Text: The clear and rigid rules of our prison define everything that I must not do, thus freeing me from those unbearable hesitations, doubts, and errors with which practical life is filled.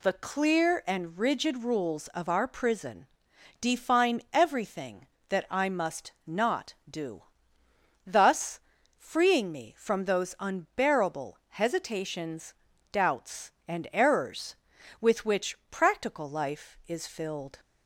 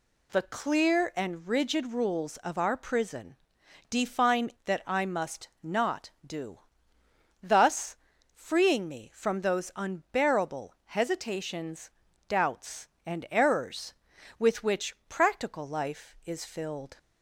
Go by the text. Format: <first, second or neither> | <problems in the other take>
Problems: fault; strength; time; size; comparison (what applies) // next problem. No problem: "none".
first | pauses between "prison" and "define"; noticeable; at 3.3 s; 0.54 s long; noticeable in the first // skips "everything"; at 4.5 s // pauses between "thus" and "freeing"; at 7.9 s; 0.38 s long; also in the first